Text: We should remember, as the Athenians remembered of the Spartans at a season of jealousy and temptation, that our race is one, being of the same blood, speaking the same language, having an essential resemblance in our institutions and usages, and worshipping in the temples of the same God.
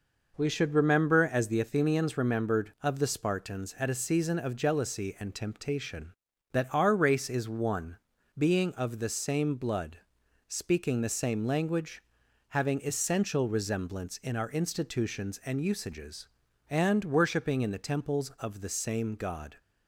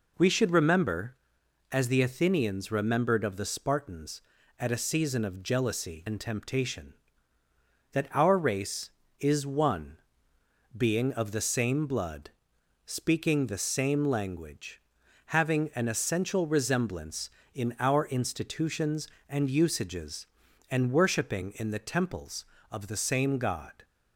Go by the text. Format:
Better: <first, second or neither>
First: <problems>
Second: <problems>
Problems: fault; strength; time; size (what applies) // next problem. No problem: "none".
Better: second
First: skips "an"; at 12.8 s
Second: none